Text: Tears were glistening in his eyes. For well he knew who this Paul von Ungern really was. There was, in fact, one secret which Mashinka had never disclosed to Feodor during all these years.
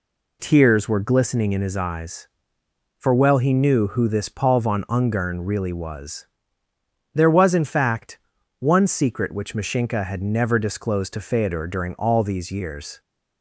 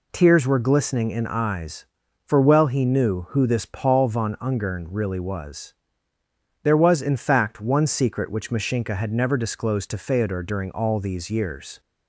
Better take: first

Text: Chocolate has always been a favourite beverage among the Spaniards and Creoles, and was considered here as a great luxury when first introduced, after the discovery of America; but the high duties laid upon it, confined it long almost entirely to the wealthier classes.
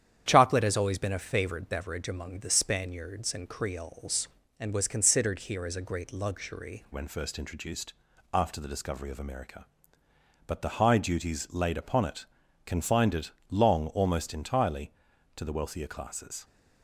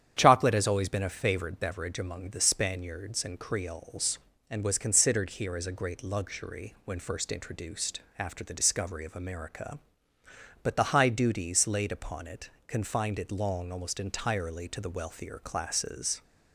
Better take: second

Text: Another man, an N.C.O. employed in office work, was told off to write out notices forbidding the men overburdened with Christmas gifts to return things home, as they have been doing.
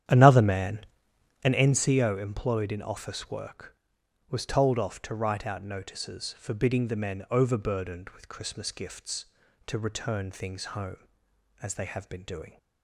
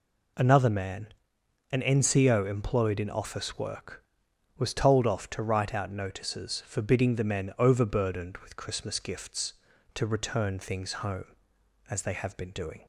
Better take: second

